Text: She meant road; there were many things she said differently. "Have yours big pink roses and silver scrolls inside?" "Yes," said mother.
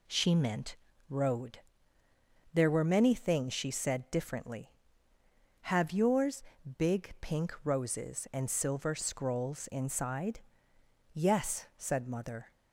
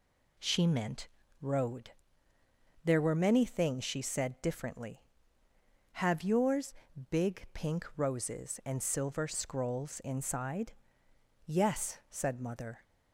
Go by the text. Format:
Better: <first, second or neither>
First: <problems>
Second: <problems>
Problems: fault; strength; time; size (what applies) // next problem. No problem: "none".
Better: neither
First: pauses between "meant" and "road"; slight; at 0.7 s; 0.32 s long // pauses between "yours" and "big"; slight; at 6.4 s; 0.32 s long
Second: pauses between "meant" and "road"; slight; at 1.0 s; 0.32 s long // pauses between "yours" and "big"; slight; at 6.7 s; 0.34 s long